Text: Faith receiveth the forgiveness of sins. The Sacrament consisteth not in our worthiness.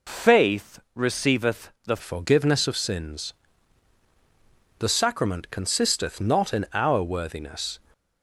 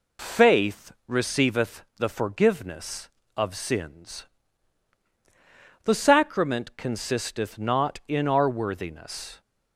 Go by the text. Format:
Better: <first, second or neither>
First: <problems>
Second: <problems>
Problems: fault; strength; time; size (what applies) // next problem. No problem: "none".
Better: second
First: pauses between "Faith" and "receiveth"; slight; at 0.7 s; 0.16 s long // changes voice at "forgiveness"; from 2.0 s on; 5.7 s long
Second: pauses between "Faith" and "receiveth"; slight; at 0.9 s; 0.16 s long